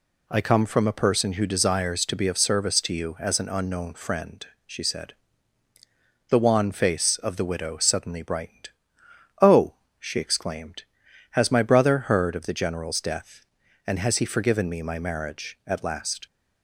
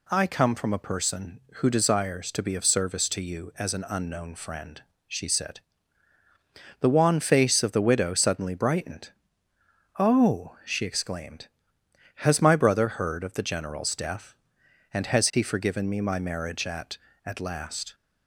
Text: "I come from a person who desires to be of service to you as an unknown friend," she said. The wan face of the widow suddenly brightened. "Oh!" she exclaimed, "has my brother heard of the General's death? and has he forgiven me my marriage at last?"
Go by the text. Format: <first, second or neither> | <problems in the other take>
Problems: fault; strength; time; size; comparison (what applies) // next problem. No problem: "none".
first | says "at" twice; at 17.2 s